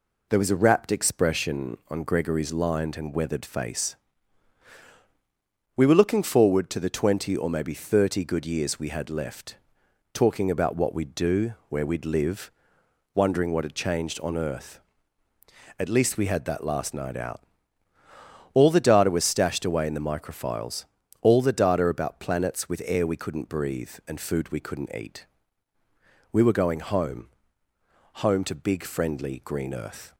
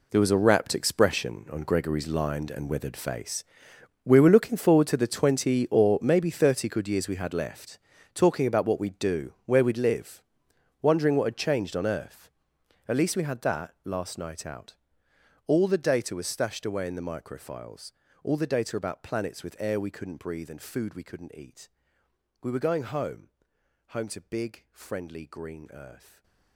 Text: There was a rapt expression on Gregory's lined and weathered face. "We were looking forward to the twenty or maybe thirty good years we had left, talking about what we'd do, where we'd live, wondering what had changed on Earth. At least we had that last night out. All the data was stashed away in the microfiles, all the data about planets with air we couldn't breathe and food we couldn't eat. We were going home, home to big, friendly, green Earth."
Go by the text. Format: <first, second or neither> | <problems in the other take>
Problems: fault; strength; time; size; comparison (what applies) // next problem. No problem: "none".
first | gets quieter; strong; throughout; 15.5 dB // stays silent after the last word; slight; from 25.9 s on; 0.6 s long